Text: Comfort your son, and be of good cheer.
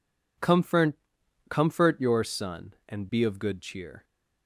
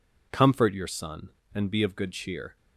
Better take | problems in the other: second | says "Comfort" twice; at 1.4 s

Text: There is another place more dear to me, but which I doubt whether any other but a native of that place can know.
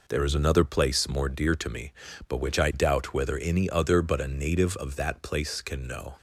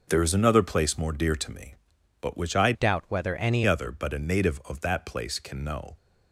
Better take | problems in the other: first | changes voice from "doubt" to "any"; from 2.7 to 3.6 s; 0.9 s long

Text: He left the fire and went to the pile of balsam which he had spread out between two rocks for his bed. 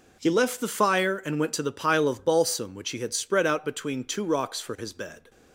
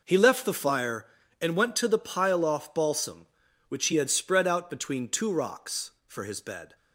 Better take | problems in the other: first | says "off" for "of"; at 2.4 s

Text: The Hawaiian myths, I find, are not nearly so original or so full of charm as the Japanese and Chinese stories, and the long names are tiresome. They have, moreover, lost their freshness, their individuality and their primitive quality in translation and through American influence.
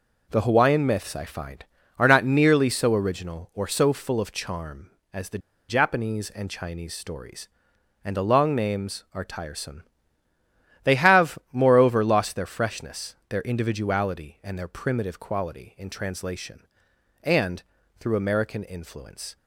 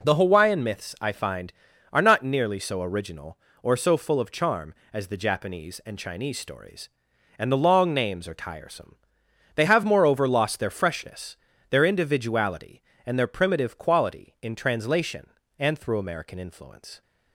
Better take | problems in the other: second | pauses between "the" and "Japanese"; slight; at 5.3 s; 0.31 s long // pauses between "and" and "through"; at 17.6 s; 0.38 s long

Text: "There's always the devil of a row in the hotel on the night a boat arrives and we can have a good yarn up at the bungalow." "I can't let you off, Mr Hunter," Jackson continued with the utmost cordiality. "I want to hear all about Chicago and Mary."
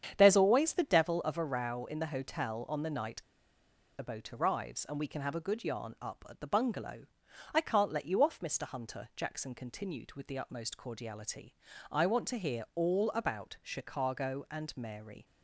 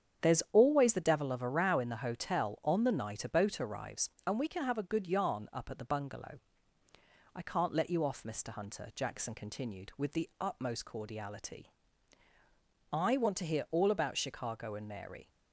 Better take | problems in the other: second | starts louder than the rest; strong; until 1.1 s; 8.5 dB; strong in the second // pauses between "night" and "a"; noticeable; at 3.2 s; 0.74 s long

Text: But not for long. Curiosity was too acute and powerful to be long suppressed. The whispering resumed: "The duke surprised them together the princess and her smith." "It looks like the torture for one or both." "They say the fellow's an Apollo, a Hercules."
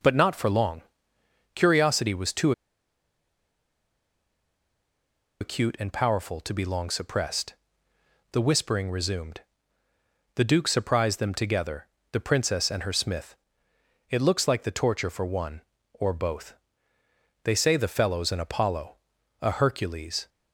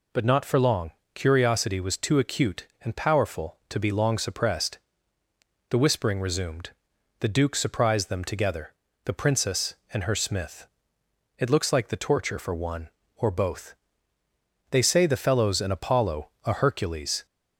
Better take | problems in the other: second | pauses between "too" and "acute"; strong; at 2.5 s; 2.8 s long // pauses between "together" and "the"; slight; at 11.8 s; 0.26 s long; slight in the second

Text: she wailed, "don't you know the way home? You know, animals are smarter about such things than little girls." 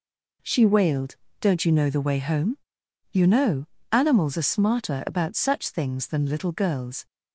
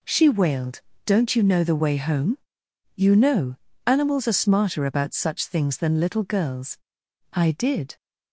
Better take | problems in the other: first | goes on to say "I did"; noticeable; from 7.3 s on; 0.64 s long

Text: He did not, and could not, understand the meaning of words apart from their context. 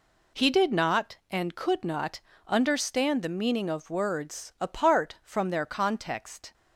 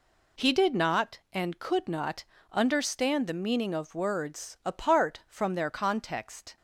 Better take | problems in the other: neither | none

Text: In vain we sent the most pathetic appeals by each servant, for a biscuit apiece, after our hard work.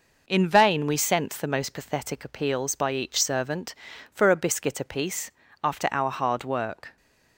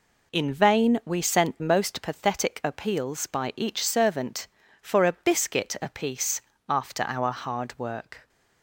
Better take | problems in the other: first | skips "the"; at 1.6 s

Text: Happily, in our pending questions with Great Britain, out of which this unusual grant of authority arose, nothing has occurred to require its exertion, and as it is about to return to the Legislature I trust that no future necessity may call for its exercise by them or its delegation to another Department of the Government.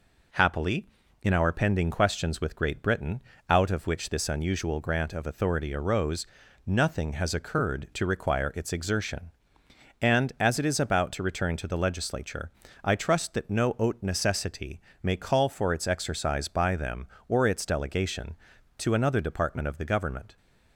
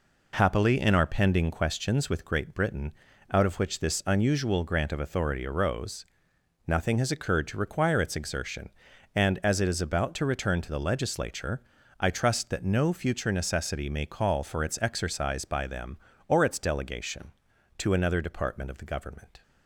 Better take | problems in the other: second | pauses between "Legislature" and "I"; slight; at 12.5 s; 0.34 s long; also in the second // says "haute" for "future"; at 13.7 s // pauses between "necessity" and "may"; slight; at 14.8 s; 0.22 s long

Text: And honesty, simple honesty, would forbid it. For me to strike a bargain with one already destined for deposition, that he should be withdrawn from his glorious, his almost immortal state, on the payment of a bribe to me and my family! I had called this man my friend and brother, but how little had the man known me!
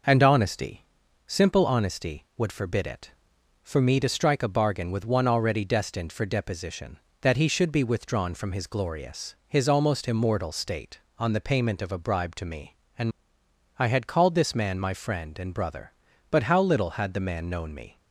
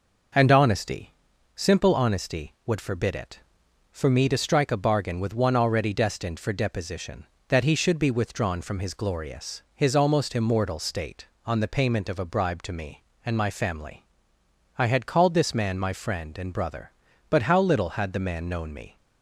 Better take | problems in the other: second | skips "my family"; at 13.4 s

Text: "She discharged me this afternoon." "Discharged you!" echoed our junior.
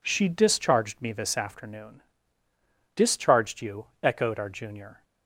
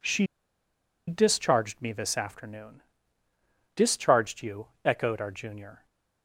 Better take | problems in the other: first | pauses between "She" and "discharged"; noticeable; at 0.2 s; 0.81 s long

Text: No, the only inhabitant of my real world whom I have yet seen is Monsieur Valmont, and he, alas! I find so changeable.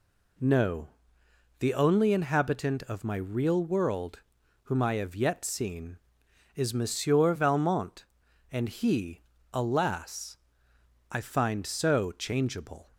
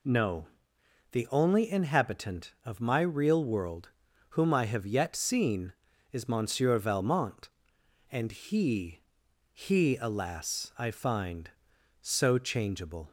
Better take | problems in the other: first | pauses between "world" and "whom"; at 3.8 s; 0.40 s long; also in the first // says "he" twice; at 9.5 s

